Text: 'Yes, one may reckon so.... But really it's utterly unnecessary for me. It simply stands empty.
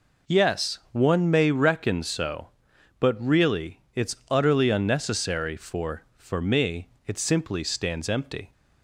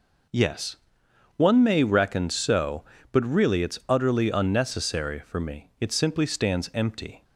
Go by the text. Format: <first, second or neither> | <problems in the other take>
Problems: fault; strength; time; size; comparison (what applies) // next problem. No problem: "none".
second | says "for" twice; at 6.1 s